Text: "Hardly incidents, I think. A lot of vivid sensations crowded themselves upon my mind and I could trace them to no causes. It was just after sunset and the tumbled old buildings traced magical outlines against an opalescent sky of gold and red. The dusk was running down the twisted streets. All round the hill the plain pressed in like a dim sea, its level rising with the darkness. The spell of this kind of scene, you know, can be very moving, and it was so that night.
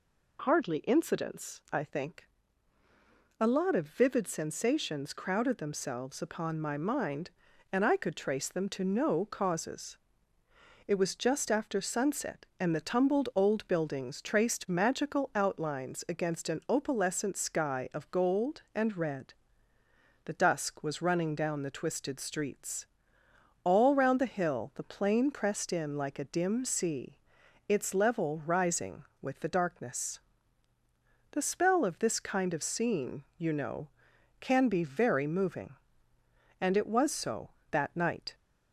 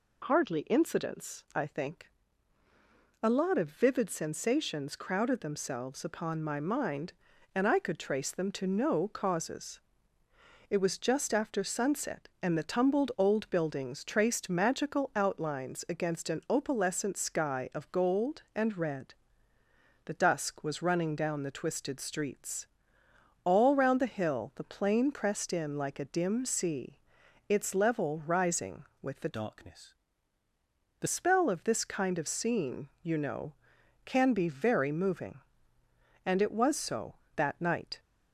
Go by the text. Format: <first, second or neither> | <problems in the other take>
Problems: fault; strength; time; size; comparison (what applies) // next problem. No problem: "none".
first | changes voice from "darkness" to "The"; from 29.3 to 31.0 s; 1.7 s long